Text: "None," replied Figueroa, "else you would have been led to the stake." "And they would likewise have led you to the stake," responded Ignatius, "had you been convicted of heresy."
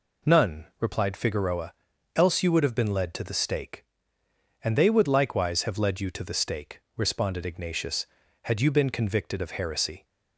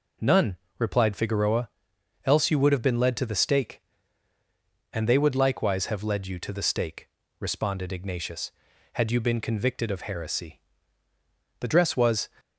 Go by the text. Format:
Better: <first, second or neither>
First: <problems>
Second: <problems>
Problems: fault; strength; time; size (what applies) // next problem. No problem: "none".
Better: first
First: none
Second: goes on to say "The dress was"; noticeable; from 11.6 s on; 0.68 s long